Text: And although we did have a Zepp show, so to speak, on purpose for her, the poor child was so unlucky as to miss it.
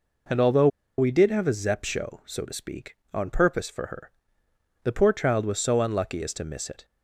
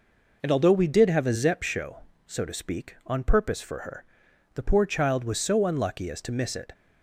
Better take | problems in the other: second | pauses between "although" and "we"; slight; at 0.6 s; 0.31 s long

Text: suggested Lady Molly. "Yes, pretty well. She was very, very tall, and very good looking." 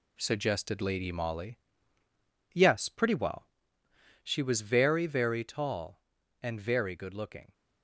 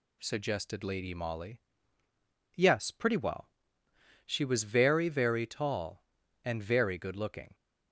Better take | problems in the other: second | gets quieter; throughout; 6.5 dB

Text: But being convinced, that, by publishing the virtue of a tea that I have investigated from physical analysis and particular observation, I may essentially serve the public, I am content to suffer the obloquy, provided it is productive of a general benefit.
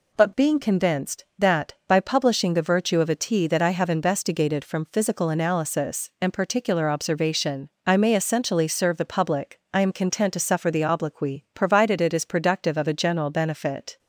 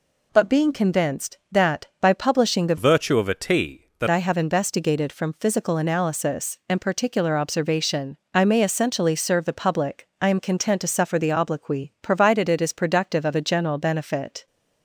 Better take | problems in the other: first | changes voice from "virtue" to "that"; from 2.7 to 4.0 s; 1.3 s long

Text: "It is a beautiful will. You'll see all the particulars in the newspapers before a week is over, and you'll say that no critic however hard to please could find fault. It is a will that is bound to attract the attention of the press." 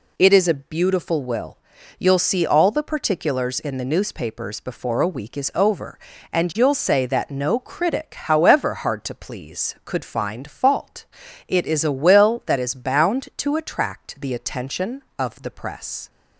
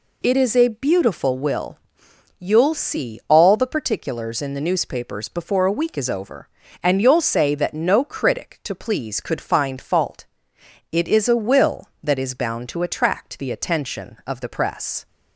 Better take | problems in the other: first | skips "however hard"; at 8.6 s

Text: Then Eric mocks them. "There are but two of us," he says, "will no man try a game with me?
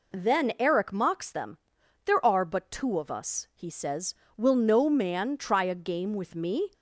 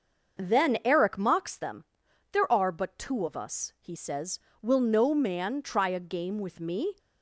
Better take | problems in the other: first | starts louder than the rest; until 1.7 s; 6.5 dB

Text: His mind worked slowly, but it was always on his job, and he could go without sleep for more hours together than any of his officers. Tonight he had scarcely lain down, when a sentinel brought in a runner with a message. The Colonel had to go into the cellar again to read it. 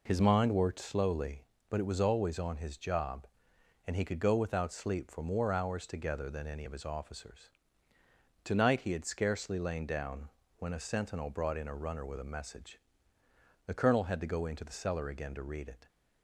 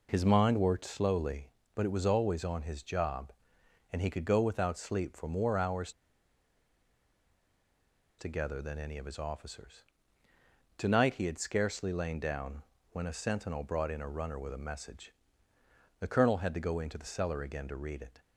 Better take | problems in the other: first | pauses between "hours" and "together"; strong; at 5.9 s; 2.2 s long

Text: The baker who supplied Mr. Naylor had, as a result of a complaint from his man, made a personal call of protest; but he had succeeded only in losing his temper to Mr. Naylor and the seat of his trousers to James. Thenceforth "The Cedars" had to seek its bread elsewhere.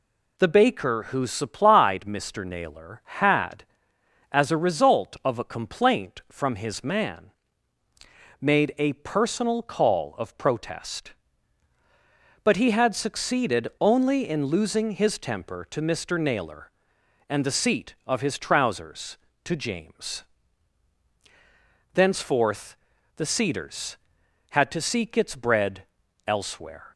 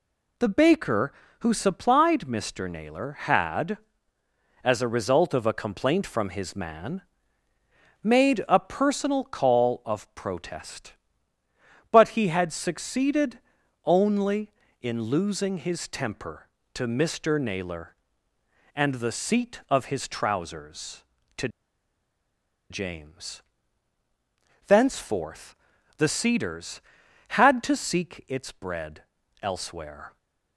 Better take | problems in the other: first | pauses between "succeeded" and "only"; noticeable; at 13.3 s; 0.46 s long // pauses between "to" and "James"; at 21.4 s; 1.2 s long // pauses between "Thenceforth" and "The"; at 25.5 s; 0.44 s long; also in the first // pauses between "bread" and "elsewhere"; at 29.0 s; 0.38 s long; also in the first

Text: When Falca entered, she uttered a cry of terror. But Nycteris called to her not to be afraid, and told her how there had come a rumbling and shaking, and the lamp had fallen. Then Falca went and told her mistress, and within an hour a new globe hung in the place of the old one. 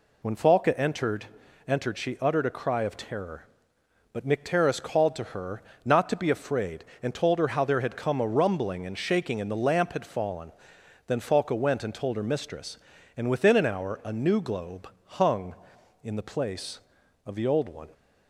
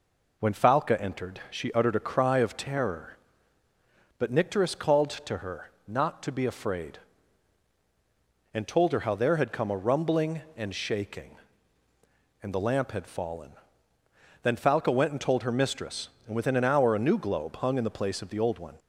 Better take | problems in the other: second | says "entered" twice; at 1.6 s // pauses between "her" and "not"; slight; at 5.6 s; 0.24 s long; slight in the second // pauses between "globe" and "hung"; slight; at 14.8 s; 0.20 s long

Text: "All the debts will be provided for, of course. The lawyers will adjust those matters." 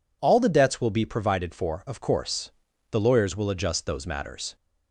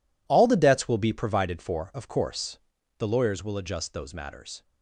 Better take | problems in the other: first | gets quieter; strong; throughout; 13.5 dB

